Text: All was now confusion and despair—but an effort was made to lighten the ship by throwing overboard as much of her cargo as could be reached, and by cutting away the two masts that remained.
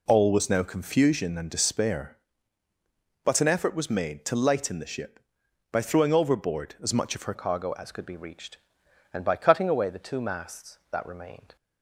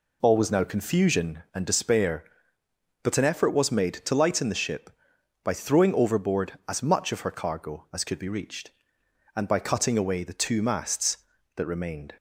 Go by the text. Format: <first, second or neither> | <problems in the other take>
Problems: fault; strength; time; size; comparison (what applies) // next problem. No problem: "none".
second | changes voice at "cargo"; from 7.3 s on; 4.2 s long